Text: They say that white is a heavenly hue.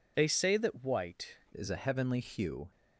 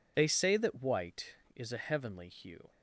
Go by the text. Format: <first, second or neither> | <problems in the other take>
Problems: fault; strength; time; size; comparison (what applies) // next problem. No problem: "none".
second | changes voice at "is"; from 1.5 s on; 1.2 s long